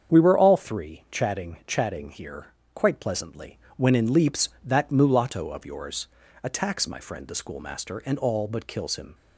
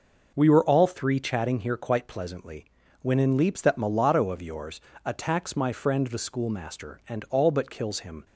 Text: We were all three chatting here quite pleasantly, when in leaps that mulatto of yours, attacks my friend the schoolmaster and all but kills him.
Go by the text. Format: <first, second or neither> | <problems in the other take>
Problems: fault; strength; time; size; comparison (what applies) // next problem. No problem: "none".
second | starts louder than the rest; strong; until 1.1 s; 7.5 dB // says "chatting" twice; at 1.6 s // pauses between "here" and "quite"; slight; at 2.4 s; 0.28 s long